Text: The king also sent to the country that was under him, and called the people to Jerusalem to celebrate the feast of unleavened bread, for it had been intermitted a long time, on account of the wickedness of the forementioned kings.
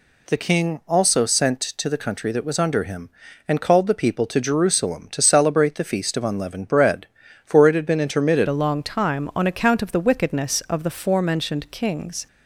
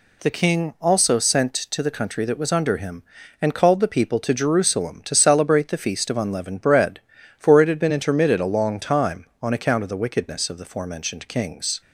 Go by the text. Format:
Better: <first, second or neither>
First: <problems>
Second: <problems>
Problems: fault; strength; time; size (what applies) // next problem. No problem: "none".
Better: second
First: changes voice at "a"; from 8.4 s on; 3.8 s long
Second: none